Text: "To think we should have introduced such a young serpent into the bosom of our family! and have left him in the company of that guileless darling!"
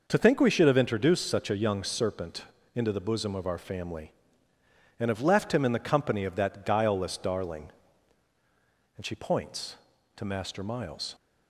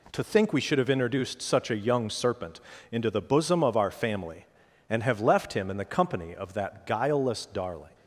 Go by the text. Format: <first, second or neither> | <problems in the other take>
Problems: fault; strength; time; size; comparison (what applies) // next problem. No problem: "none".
second | pauses between "serpent" and "into"; slight; at 2.4 s; 0.30 s long; slight in the second // goes on to say "and she points to Master Miles"; strong; from 8.9 s on; 2.2 s long